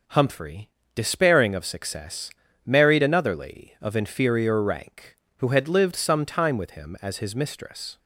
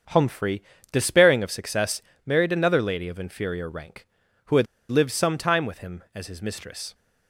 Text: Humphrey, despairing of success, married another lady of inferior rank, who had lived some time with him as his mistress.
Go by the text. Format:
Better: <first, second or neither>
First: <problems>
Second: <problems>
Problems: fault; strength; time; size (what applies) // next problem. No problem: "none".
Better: first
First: none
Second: starts louder than the rest; until 1.3 s; 7 dB // pauses between "had" and "lived"; slight; at 4.6 s; 0.24 s long